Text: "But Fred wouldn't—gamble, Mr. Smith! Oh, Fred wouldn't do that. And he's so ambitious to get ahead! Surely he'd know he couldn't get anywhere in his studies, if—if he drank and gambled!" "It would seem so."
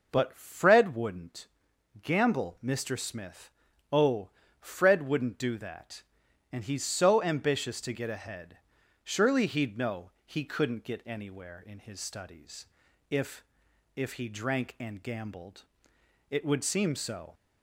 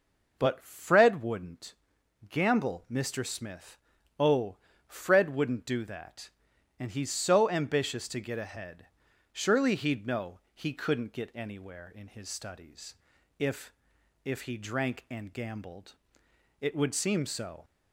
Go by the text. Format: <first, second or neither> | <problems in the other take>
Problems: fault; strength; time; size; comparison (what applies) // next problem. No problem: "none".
neither | none